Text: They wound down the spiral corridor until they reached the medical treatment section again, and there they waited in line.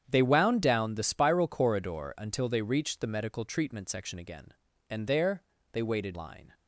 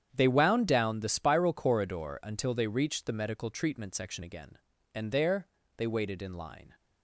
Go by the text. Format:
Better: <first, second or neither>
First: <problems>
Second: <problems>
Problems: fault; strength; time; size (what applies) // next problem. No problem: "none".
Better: second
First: starts louder than the rest; strong; until 1.0 s; 8.5 dB // pauses between "there" and "they"; slight; at 5.4 s; 0.30 s long // skips "in"; at 6.1 s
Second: starts louder than the rest; strong; until 1.1 s; 8.5 dB // pauses between "there" and "they"; slight; at 5.4 s; 0.30 s long